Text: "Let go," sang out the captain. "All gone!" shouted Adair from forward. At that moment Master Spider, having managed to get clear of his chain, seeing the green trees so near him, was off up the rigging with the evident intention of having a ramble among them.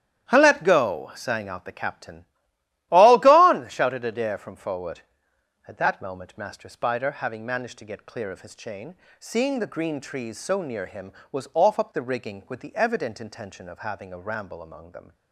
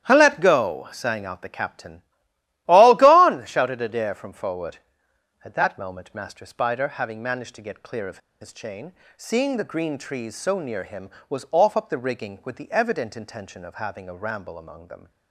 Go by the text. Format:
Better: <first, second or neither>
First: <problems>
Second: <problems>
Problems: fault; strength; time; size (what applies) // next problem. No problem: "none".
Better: first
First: starts louder than the rest; strong; until 1.3 s; 11 dB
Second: starts louder than the rest; strong; until 1.1 s; 11 dB // pauses between "of" and "his"; slight; at 8.1 s; 0.23 s long